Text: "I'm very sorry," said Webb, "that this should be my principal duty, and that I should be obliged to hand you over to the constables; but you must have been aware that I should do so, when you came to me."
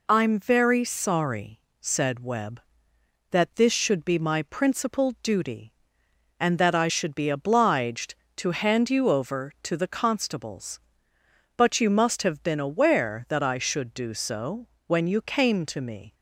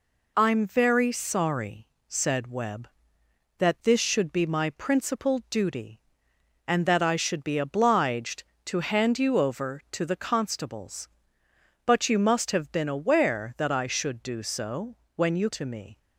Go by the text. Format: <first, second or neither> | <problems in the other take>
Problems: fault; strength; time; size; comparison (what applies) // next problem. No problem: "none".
first | skips "came"; at 15.5 s